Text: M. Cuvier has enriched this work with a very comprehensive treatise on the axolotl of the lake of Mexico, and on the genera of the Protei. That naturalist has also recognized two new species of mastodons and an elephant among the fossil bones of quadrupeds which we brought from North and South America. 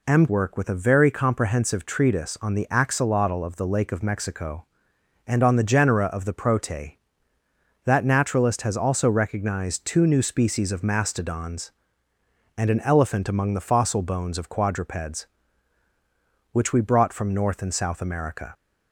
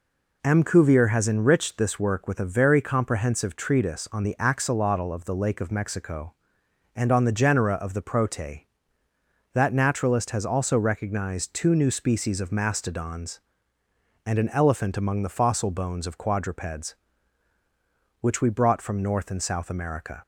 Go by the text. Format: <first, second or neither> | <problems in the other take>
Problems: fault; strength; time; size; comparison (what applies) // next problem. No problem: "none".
second | skips "Cuvier has enriched this"; at 0.2 s